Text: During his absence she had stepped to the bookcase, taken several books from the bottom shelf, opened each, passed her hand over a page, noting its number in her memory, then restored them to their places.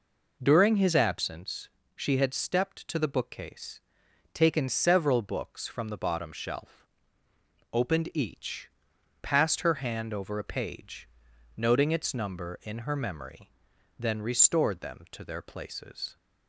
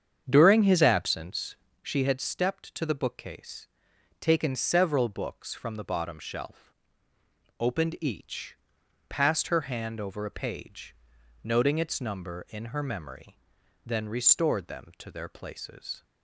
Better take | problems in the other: first | starts louder than the rest; strong; until 2.0 s; 7.5 dB // pauses between "absence" and "she"; slight; at 1.5 s; 0.26 s long; slight in the first

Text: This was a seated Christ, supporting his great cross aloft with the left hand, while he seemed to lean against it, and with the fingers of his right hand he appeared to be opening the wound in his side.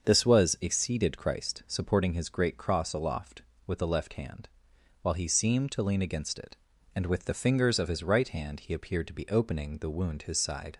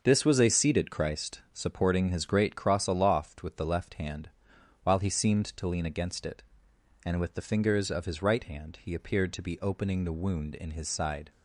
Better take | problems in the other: second | starts louder than the rest; until 1.1 s; 7 dB; also in the second // skips "in"; at 10.2 s

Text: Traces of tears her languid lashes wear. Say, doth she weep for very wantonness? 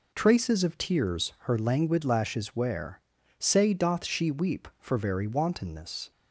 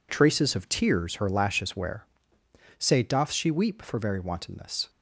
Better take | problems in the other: first | skips "languid"; at 1.2 s

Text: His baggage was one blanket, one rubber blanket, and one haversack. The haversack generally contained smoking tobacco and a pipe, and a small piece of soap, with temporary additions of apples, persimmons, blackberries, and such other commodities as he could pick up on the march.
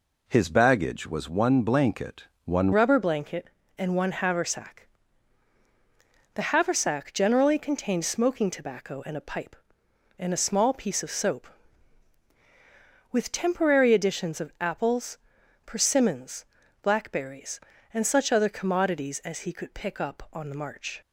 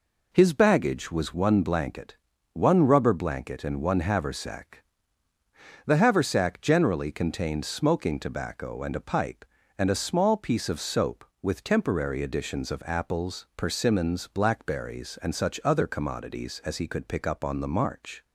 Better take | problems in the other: second | changes voice at "rubber"; from 2.7 s on; 18.3 s long

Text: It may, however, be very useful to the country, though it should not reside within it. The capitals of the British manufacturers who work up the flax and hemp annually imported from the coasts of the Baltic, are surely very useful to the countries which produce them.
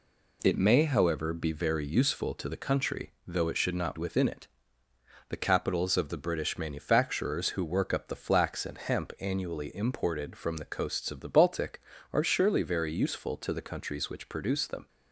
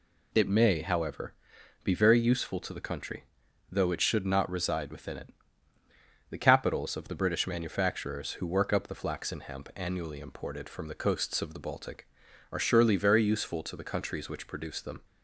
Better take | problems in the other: second | skips "reside"; at 3.9 s

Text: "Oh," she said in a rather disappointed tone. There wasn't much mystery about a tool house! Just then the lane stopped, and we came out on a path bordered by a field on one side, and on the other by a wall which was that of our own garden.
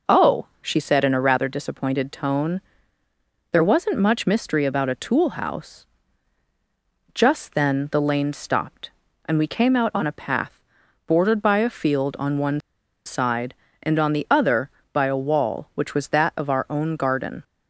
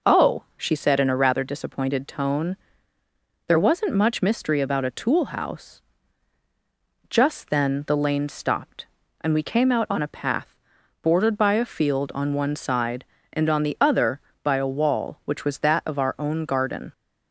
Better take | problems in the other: second | pauses between "path" and "bordered"; noticeable; at 10.5 s; 0.46 s long; noticeable in the second // pauses between "one" and "side"; at 12.5 s; 0.45 s long

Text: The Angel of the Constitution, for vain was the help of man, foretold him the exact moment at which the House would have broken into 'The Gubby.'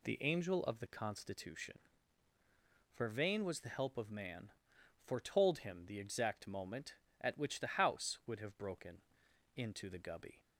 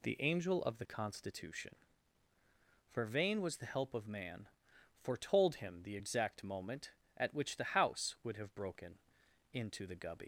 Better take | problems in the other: first | pauses between "broken" and "into"; noticeable; at 8.9 s; 0.54 s long; noticeable in the first // leaves "Gubby" unfinished; at 10.2 s; 90 ms

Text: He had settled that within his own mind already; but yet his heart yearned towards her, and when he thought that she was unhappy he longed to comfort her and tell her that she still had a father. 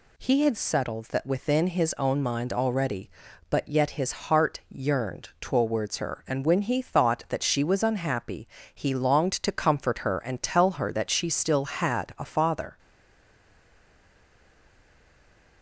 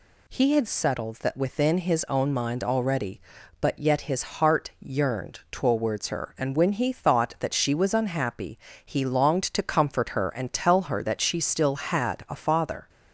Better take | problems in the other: second | pauses between "unhappy" and "he"; slight; at 8.4 s; 0.26 s long; slight in the second // stays silent after the last word; strong; from 12.7 s on; 2.9 s long

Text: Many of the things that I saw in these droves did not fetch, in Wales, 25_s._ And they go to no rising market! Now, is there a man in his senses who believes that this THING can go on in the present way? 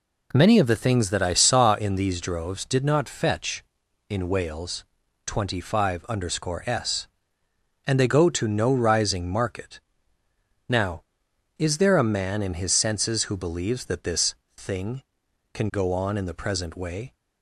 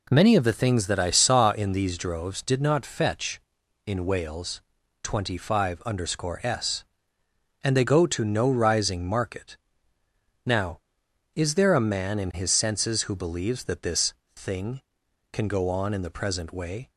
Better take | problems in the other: neither | pauses between "this" and "THING"; slight; the same in both

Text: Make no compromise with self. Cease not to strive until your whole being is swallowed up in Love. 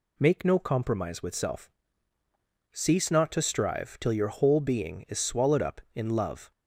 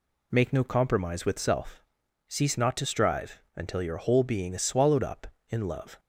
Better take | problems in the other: second | says "till" for "until"; at 3.9 s

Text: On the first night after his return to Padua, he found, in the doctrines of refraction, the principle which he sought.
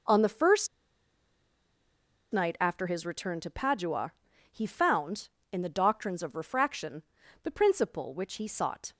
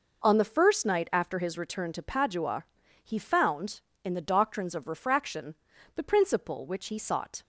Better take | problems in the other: second | pauses between "first" and "night"; strong; at 0.6 s; 1.6 s long

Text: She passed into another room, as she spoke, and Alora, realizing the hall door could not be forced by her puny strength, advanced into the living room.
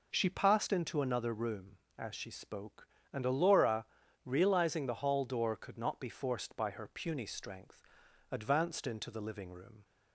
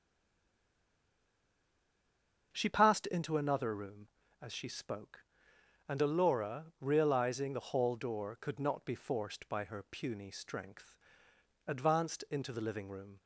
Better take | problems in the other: first | stays silent before the first word; strong; until 2.5 s; 2.5 s long // starts louder than the rest; until 3.5 s; 6.5 dB

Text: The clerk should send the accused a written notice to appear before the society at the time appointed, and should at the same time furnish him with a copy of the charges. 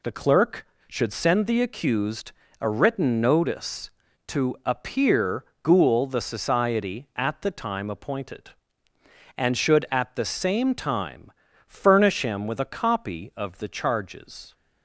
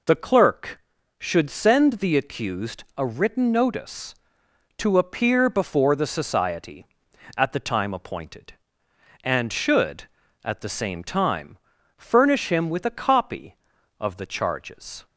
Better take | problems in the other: second | pauses between "accused" and "a"; slight; at 2.3 s; 0.28 s long // says "ghoul" for "before"; at 5.6 s // pauses between "time" and "furnish"; slight; at 11.3 s; 0.34 s long; also in the second

